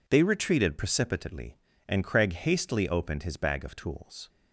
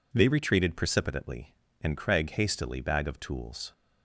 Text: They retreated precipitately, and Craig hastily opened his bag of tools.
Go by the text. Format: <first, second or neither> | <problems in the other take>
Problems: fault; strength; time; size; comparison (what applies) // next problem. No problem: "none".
first | skips "opened his"; at 2.8 s